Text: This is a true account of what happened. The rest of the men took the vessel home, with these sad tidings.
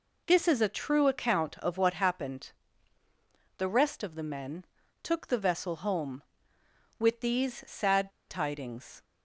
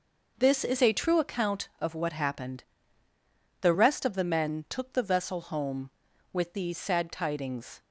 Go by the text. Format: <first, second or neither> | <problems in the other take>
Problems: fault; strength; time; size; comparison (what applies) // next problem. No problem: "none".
second | pauses between "men" and "took"; at 4.6 s; 0.38 s long // pauses between "sad" and "tidings"; slight; at 8.0 s; 0.19 s long